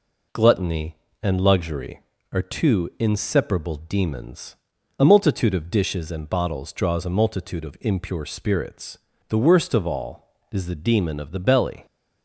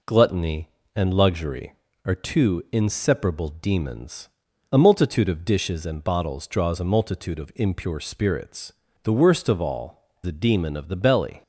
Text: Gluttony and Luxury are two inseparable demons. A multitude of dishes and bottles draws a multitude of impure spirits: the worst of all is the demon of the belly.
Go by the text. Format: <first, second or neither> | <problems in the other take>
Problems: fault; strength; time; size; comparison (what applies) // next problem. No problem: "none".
first | skips "is"; at 10.1 s